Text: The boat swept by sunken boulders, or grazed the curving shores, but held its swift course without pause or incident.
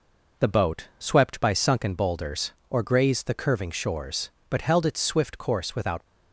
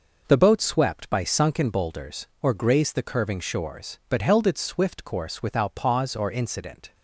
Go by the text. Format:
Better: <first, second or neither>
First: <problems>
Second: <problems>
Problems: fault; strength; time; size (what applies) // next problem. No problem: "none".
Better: second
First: stops before "pause or incident"; at 6.0 s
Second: none